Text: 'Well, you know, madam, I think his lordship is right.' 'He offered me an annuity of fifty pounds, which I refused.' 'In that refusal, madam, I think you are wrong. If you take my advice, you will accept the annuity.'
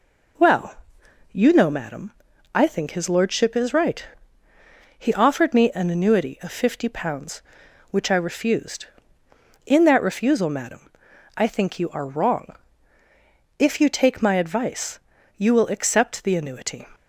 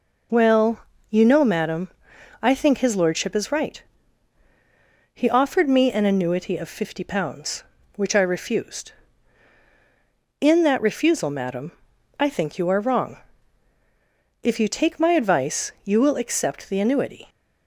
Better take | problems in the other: neither | none

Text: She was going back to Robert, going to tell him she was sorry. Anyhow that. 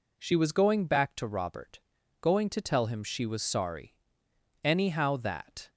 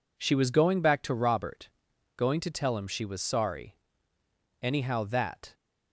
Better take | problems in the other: neither | none

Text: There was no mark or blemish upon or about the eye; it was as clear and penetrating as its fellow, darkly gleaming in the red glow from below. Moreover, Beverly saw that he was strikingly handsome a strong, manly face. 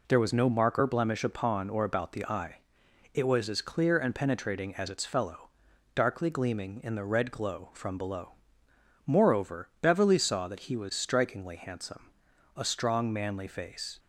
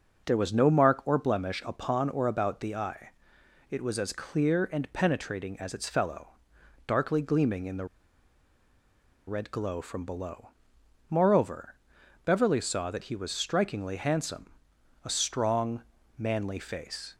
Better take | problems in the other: first | pauses between "the" and "red"; strong; at 7.8 s; 1.4 s long // pauses between "handsome" and "a"; noticeable; at 14.5 s; 0.54 s long; noticeable in the first

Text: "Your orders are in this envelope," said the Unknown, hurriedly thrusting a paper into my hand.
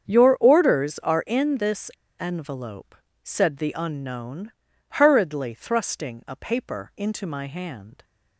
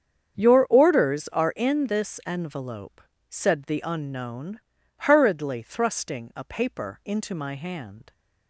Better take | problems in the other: second | starts louder than the rest; strong; until 1.1 s; 7.5 dB; strong in the second // pauses between "this" and "envelope"; slight; at 1.9 s; 0.29 s long

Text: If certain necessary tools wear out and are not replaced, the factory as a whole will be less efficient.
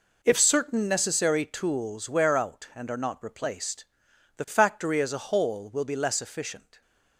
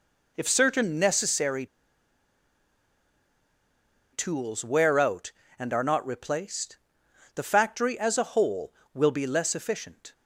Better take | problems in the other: first | pauses between "necessary" and "tools"; strong; at 1.6 s; 2.4 s long

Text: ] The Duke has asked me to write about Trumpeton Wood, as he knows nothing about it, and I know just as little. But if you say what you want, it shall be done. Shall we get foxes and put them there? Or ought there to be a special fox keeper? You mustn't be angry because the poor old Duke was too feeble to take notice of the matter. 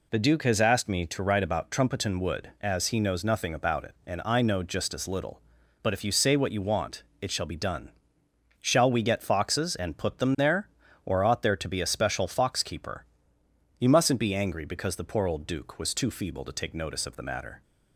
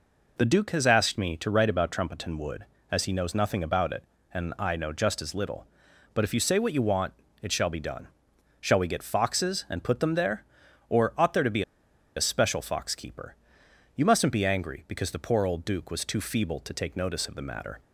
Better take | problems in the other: first | pauses between "be" and "a"; noticeable; at 11.6 s; 0.53 s long

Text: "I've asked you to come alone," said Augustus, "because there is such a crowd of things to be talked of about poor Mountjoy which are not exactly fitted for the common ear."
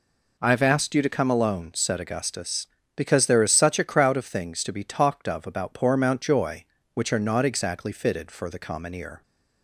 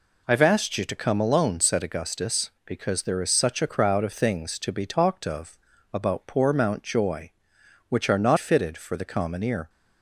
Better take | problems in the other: first | pauses between "of" and "about"; slight; at 5.5 s; 0.34 s long // skips "exactly"; at 8.3 s

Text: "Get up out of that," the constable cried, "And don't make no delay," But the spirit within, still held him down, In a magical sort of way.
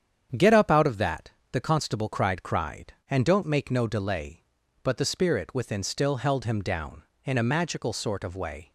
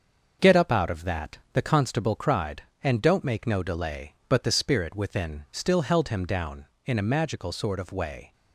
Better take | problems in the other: second | starts louder than the rest; strong; until 1.5 s; 8.5 dB; also in the second // says "cried" twice; at 2.4 s

